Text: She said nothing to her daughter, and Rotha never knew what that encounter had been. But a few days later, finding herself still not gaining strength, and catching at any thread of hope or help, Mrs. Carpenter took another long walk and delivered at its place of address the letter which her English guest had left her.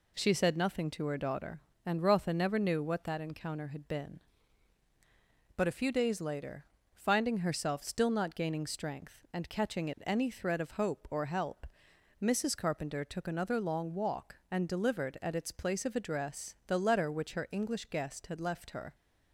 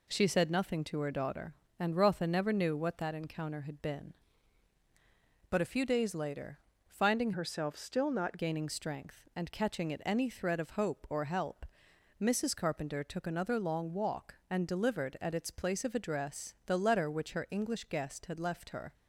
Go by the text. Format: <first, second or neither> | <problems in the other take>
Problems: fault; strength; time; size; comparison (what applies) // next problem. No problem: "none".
first | changes voice from "herself" to "not"; from 7.3 to 8.3 s; 1.0 s long